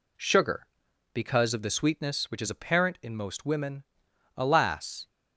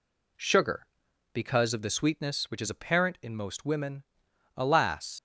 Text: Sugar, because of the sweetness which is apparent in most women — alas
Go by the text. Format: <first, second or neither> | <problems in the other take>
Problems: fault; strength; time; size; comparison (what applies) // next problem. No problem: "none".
first | leaves "alas" unfinished; at 5.1 s; 80 ms